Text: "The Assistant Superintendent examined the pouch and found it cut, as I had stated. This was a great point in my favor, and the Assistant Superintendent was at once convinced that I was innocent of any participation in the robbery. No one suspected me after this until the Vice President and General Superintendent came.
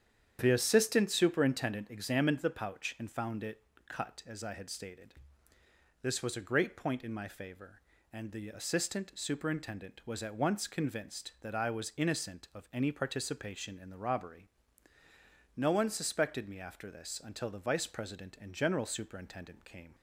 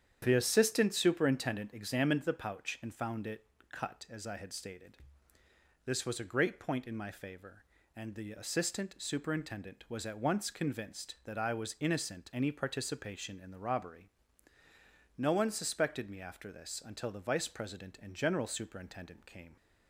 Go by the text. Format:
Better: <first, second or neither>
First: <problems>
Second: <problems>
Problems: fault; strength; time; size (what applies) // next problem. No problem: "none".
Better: first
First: starts louder than the rest; strong; until 1.4 s; 9 dB // pauses between "it" and "cut"; slight; at 3.6 s; 0.22 s long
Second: starts louder than the rest; strong; until 1.2 s; 9 dB // pauses between "it" and "cut"; slight; at 3.4 s; 0.22 s long // skips "of"; at 12.3 s